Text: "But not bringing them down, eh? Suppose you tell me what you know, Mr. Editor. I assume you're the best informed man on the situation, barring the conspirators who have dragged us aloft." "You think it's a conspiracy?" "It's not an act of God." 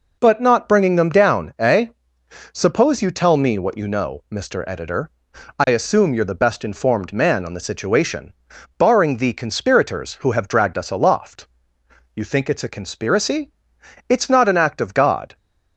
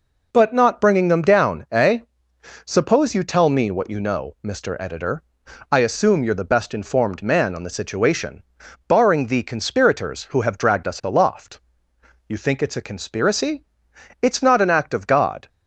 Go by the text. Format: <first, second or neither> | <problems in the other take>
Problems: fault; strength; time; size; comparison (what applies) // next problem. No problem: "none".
neither | none